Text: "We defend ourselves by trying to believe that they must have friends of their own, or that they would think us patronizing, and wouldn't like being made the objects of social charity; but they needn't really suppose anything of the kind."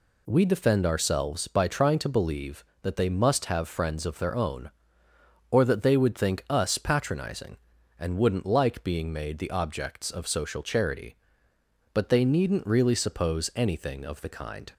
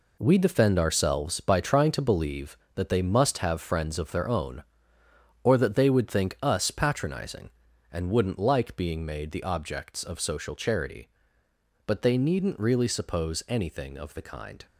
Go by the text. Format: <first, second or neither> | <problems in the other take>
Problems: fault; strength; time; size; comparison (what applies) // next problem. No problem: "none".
first | gets quieter; strong; throughout; 8.5 dB